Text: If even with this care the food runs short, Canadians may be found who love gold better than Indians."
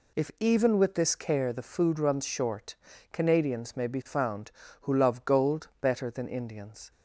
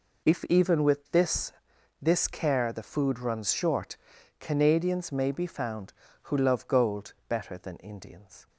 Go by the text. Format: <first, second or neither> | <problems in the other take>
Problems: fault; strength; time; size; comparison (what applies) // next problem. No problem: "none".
first | says "this" twice; at 2.0 s // pauses between "gold" and "better"; slight; at 7.1 s; 0.16 s long